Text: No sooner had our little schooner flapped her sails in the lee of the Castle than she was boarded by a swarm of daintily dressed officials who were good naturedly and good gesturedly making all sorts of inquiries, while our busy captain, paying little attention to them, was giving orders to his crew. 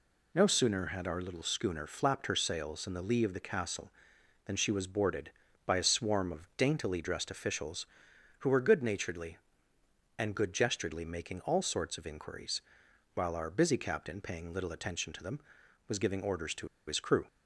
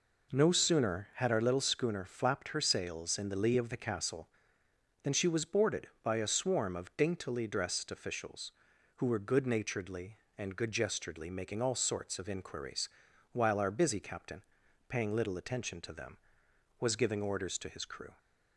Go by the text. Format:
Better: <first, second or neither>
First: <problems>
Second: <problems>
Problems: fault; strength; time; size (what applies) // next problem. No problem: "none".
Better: second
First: pauses between "to" and "his"; slight; at 16.6 s; 0.20 s long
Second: none